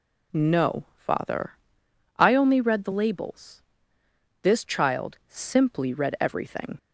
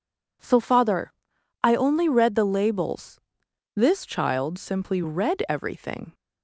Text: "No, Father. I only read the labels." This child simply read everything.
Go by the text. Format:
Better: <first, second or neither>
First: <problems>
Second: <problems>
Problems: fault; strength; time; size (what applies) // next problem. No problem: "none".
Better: first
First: none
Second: says "So" for "No"; at 0.4 s